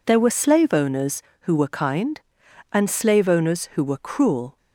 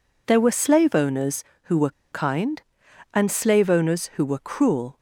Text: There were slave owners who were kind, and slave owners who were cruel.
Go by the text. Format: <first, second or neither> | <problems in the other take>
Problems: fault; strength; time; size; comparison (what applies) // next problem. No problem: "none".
first | pauses between "were" and "kind"; slight; at 1.9 s; 0.21 s long